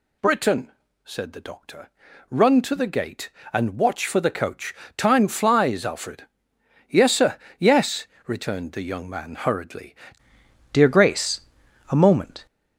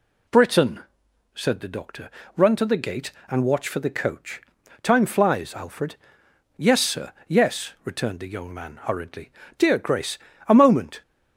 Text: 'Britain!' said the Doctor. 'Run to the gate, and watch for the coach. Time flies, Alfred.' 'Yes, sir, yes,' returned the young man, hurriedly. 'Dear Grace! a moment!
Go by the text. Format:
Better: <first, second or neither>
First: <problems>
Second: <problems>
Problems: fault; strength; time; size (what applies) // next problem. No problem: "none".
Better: second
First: changes voice at "Dear"; from 10.7 s on; 1.7 s long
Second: none